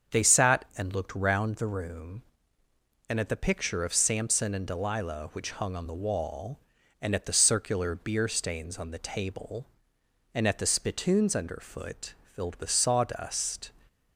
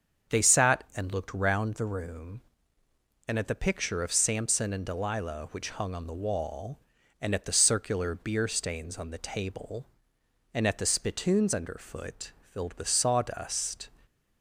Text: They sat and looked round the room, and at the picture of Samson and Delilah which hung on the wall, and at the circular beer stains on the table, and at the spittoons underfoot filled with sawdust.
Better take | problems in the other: neither | starts louder than the rest; strong; the same in both // pauses between "underfoot" and "filled"; slight; the same in both

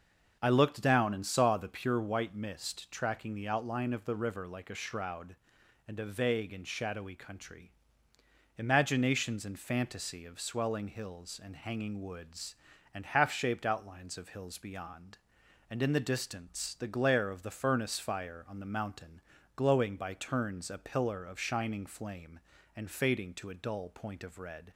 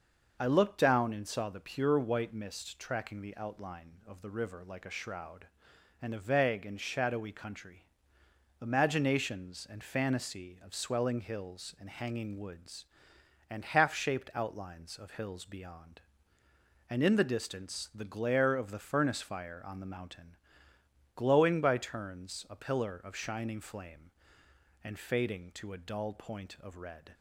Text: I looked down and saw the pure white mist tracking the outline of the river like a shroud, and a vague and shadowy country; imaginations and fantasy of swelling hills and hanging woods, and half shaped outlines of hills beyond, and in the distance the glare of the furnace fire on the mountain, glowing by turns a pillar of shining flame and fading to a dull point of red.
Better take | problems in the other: neither | starts louder than the rest; the same in both

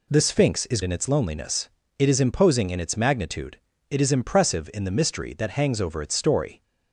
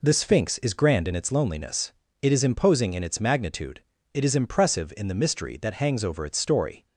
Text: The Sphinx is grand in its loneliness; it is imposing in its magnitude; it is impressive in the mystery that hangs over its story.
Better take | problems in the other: second | skips "grand"; at 0.8 s

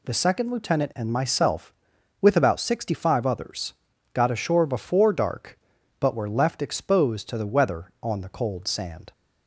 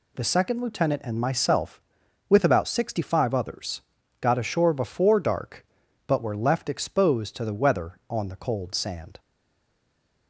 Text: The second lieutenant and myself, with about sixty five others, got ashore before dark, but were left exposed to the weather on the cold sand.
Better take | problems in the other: first | stays silent after the last word; from 9.1 s on; 1.1 s long

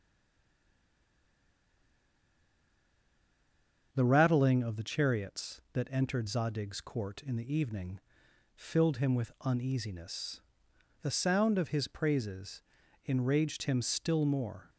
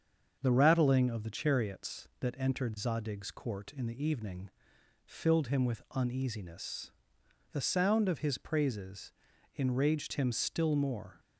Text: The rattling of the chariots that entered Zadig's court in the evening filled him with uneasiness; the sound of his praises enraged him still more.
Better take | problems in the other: second | stays silent before the first word; strong; until 3.9 s; 3.9 s long // starts louder than the rest; until 4.9 s; 7 dB; also in the second // pauses between "evening" and "filled"; noticeable; at 7.9 s; 0.56 s long; noticeable in the second // pauses between "praises" and "enraged"; noticeable; at 12.6 s; 0.46 s long; noticeable in the second

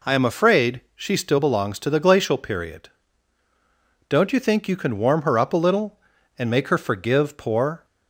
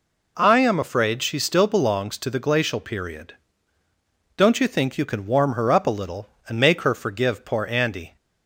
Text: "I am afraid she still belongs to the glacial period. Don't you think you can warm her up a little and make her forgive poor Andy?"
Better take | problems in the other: second | stops before "Andy"; at 7.8 s

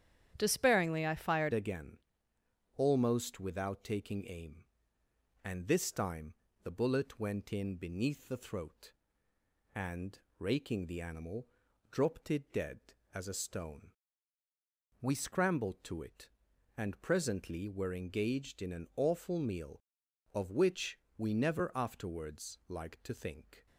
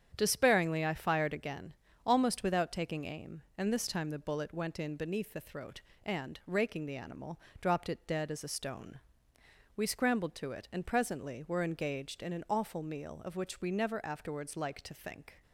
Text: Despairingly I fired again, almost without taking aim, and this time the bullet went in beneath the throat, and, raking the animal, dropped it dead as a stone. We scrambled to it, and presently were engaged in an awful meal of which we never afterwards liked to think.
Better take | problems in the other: second | starts louder than the rest; strong; until 1.3 s; 9.5 dB; strong in the second // changes voice at "again"; from 1.5 s on; 22.1 s long // pauses between "time" and "the"; slight; at 6.3 s; 0.30 s long // pauses between "which" and "we"; slight; at 20.9 s; 0.18 s long

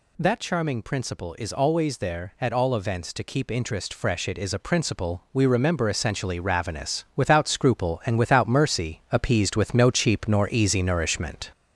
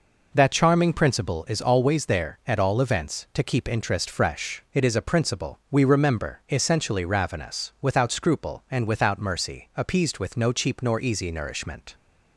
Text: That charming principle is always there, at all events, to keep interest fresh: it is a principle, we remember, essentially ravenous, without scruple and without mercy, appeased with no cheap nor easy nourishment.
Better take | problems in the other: second | gets louder; noticeable; throughout; 4.5 dB

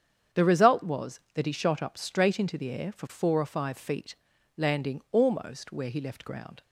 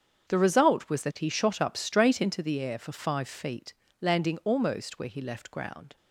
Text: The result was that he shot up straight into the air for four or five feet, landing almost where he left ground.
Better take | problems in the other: first | starts louder than the rest; strong; until 1.3 s; 7.5 dB; strong in the first // skips "four or"; at 2.9 s

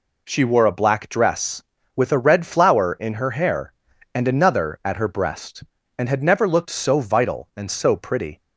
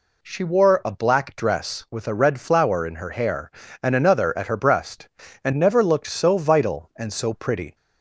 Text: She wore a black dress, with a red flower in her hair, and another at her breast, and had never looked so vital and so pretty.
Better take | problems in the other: first | skips "had"; at 5.5 s

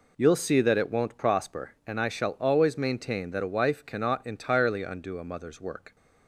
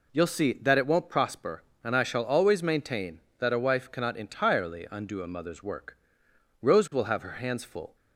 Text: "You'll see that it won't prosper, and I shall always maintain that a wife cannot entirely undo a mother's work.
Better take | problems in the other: first | goes on to say "Rose will have her hands full"; from 6.6 s on; 1.3 s long

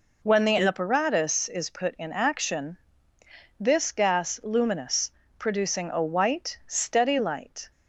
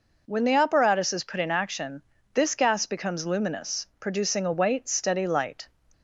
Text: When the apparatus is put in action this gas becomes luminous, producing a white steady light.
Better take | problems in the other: second | pauses between "action" and "this"; noticeable; at 2.7 s; 0.80 s long; slight in the second // skips "becomes"; at 4.4 s

